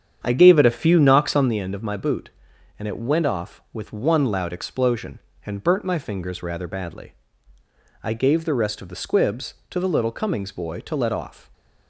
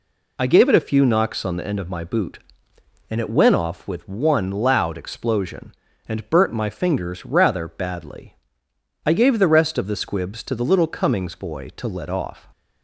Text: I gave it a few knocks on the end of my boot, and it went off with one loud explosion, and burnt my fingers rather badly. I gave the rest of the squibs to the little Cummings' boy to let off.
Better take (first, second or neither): second